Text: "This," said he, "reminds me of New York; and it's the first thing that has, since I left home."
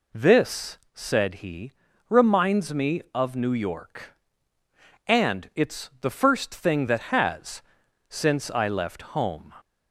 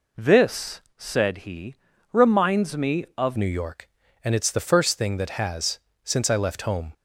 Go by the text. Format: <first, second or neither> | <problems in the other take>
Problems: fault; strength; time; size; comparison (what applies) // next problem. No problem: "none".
first | changes voice at "New"; from 3.3 s on; 3.6 s long